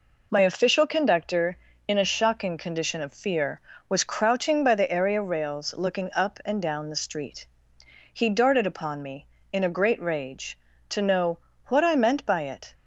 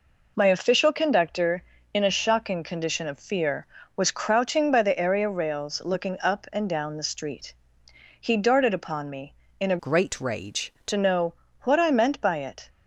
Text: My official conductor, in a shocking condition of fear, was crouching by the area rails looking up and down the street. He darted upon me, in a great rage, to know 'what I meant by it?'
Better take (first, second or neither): first